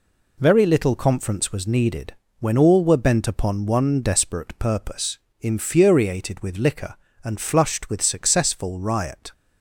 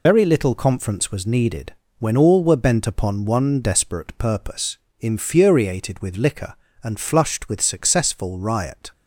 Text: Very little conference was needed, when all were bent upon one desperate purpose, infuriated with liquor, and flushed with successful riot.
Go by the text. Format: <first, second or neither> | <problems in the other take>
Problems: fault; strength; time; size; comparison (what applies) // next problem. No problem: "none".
first | loses the start of "Very"; at 0.0 s; 70 ms